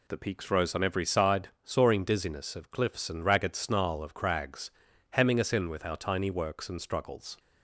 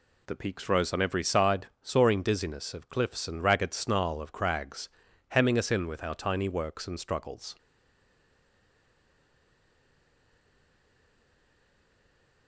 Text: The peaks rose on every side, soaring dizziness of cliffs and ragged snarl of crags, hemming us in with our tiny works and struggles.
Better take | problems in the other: first | stays silent after the last word; strong; from 7.5 s on; 4.9 s long

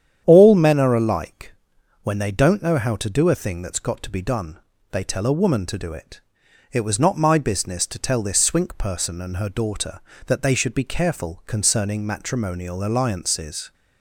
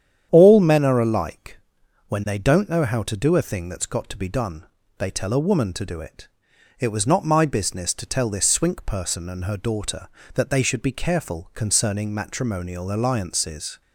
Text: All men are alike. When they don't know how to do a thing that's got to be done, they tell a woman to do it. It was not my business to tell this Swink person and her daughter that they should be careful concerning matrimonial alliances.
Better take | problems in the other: neither | starts louder than the rest; strong; the same in both

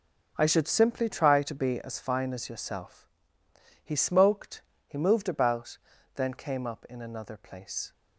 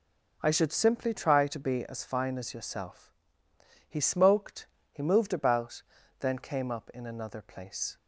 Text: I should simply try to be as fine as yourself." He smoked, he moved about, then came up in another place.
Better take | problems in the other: second | gets quieter; strong; throughout; 11.5 dB

